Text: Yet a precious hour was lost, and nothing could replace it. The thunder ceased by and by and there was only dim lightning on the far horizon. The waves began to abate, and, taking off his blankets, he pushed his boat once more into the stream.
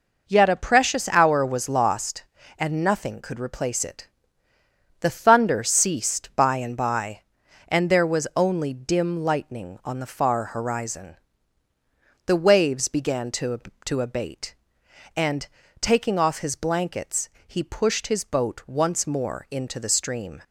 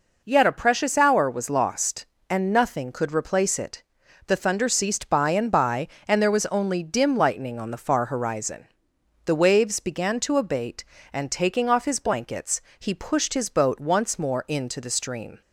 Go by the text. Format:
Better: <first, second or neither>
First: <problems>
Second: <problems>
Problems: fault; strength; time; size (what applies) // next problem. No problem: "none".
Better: second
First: says "to" twice; at 13.8 s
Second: none